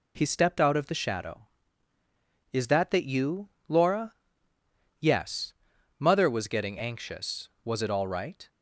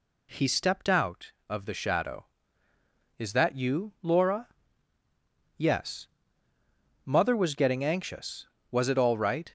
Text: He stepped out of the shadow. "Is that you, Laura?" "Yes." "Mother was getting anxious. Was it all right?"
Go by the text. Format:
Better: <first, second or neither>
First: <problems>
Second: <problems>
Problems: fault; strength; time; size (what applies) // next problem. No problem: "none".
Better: second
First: says "that" twice; at 2.9 s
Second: none